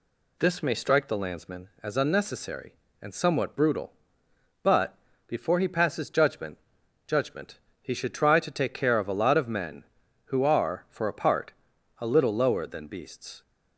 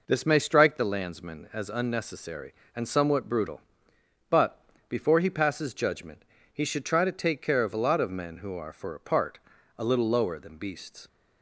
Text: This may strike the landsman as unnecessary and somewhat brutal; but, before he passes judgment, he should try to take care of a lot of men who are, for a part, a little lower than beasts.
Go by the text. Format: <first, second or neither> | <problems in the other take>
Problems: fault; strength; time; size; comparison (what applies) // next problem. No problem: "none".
second | says "judgment" twice; at 7.0 s